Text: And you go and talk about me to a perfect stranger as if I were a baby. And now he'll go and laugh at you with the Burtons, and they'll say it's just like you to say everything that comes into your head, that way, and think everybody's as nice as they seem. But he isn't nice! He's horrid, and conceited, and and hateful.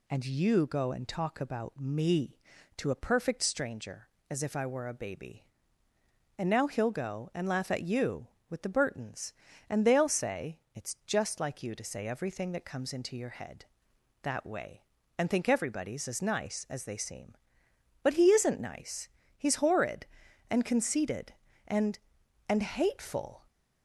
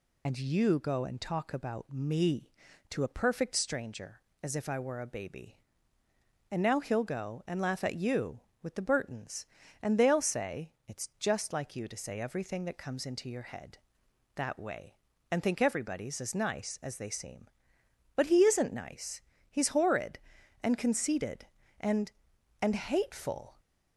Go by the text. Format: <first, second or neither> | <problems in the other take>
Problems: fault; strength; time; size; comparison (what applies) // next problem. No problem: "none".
first | loses the start of "And"; at 0.2 s; 40 ms // pauses between "say" and "it's"; slight; at 10.7 s; 0.16 s long; slight in the first